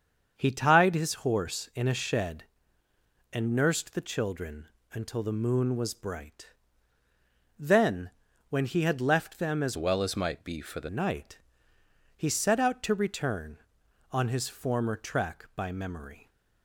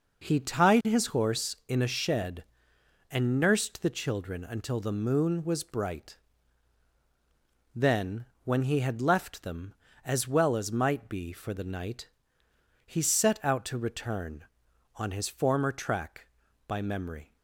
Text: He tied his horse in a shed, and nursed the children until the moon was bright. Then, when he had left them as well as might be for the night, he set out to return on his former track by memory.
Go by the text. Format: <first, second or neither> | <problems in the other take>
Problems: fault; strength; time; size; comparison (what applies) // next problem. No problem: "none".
second | starts louder than the rest; until 1.3 s; 7 dB // pauses between "children" and "until"; slight; at 4.6 s; 0.26 s long // changes voice from "well" to "the"; from 9.7 to 10.8 s; 1.1 s long